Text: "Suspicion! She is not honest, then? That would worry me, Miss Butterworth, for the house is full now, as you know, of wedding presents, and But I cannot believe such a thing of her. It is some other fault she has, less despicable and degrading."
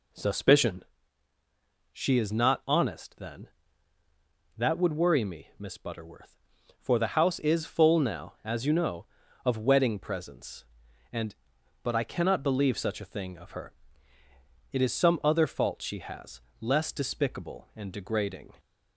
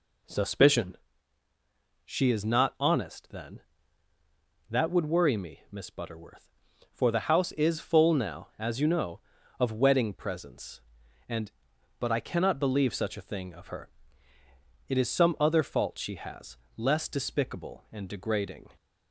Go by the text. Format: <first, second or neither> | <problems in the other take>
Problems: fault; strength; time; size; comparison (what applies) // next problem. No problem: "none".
neither | none